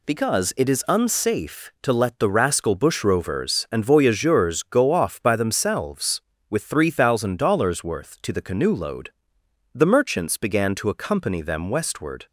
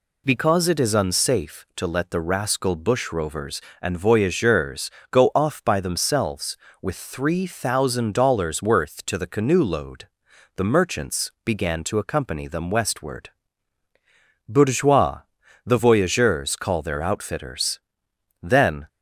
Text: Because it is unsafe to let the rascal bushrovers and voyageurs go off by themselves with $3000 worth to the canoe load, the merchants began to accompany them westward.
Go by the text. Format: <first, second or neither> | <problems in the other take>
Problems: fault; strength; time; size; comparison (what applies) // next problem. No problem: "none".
first | pauses between "voyageurs" and "go"; slight; at 4.8 s; 0.22 s long // goes on to say "Bourgeois the voyageurs call their outfitters Then"; strong; from 14.4 s on; 4.3 s long